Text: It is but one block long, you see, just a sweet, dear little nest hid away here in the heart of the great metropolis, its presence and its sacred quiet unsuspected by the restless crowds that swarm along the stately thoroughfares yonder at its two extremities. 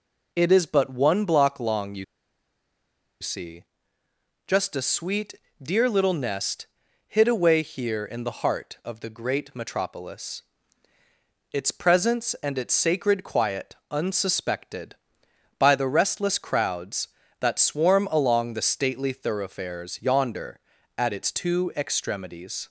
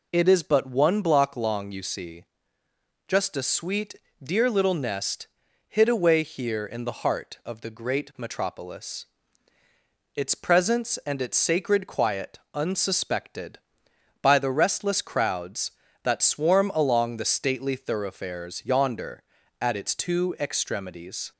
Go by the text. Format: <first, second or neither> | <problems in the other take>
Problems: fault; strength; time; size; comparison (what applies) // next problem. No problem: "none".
second | pauses between "you" and "see"; at 2.0 s; 1.1 s long // pauses between "nest" and "hid"; at 6.6 s; 0.40 s long; also in the second // pauses between "quiet" and "unsuspected"; slight; at 13.7 s; 0.16 s long; slight in the second